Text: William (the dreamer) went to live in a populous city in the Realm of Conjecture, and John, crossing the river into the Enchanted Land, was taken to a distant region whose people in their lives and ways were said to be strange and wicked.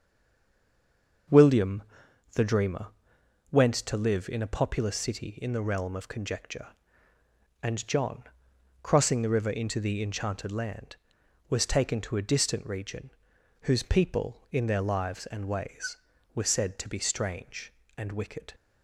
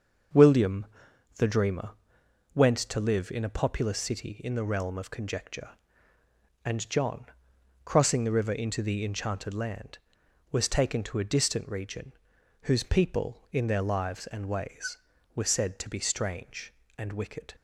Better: second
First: stays silent before the first word; noticeable; until 1.2 s; 1.2 s long // starts louder than the rest; until 2.8 s; 6 dB // pauses between "region" and "whose"; noticeable; at 13.1 s; 0.51 s long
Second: starts louder than the rest; until 1.8 s; 6 dB // pauses between "region" and "whose"; noticeable; at 12.1 s; 0.50 s long

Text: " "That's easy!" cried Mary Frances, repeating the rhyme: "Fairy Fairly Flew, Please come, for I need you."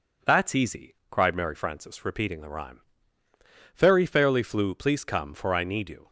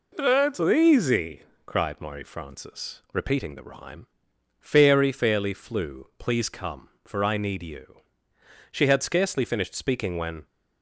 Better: first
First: none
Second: goes on to say "She had scarcely finished speaking when"; strong; from 8.7 s on; 1.7 s long

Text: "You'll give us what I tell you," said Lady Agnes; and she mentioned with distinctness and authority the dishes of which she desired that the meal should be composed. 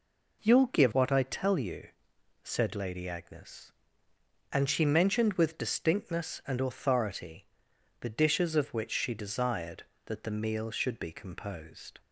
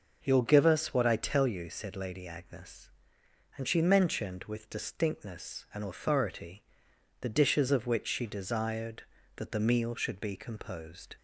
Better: second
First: skips "us"; at 0.9 s // pauses between "authority" and "the"; noticeable; at 7.4 s; 0.54 s long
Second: pauses between "authority" and "the"; noticeable; at 6.6 s; 0.58 s long

